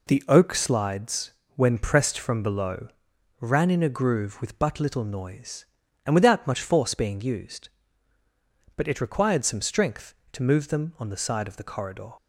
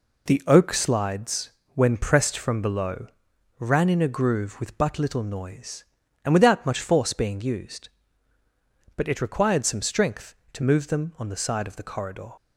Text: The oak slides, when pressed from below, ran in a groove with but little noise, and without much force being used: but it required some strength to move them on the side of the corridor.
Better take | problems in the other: neither | none

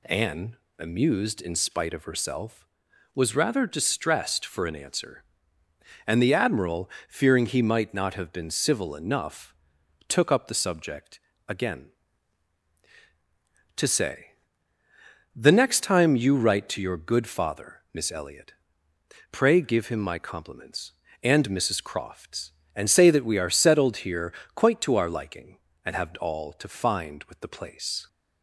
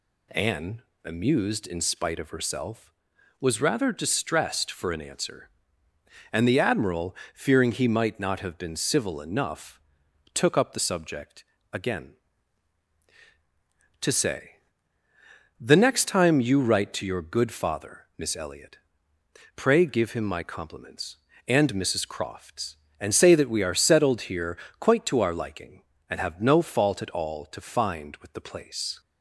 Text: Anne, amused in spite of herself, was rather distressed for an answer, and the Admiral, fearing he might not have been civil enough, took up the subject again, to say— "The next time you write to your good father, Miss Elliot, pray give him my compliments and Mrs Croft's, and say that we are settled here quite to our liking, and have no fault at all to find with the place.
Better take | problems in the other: second | pauses between "subject" and "again"; slight; at 11.1 s; 0.28 s long; slight in the second // pauses between "here" and "quite"; slight; at 24.3 s; 0.22 s long; slight in the second // skips "no fault at"; at 26.1 s

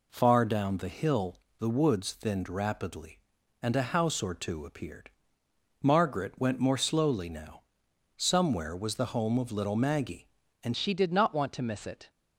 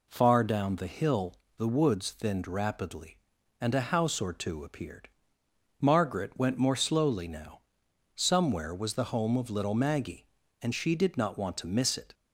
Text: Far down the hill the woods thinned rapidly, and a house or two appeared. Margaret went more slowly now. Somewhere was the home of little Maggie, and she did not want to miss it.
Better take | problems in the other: second | pauses between "hill" and "the"; slight; at 1.3 s; 0.22 s long; slight in the second // changes voice at "she"; from 10.7 s on; 1.3 s long

